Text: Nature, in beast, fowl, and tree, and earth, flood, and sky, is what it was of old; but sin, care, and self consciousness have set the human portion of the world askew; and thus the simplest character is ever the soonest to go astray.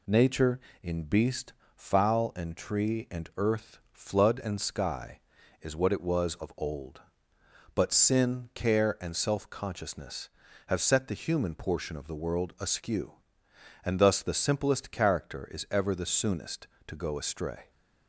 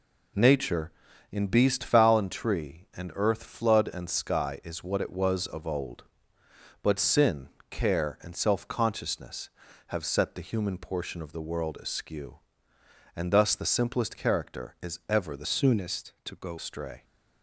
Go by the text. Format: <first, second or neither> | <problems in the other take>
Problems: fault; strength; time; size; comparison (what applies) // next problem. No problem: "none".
first | changes voice from "soonest" to "go"; from 15.4 to 16.5 s; 1.1 s long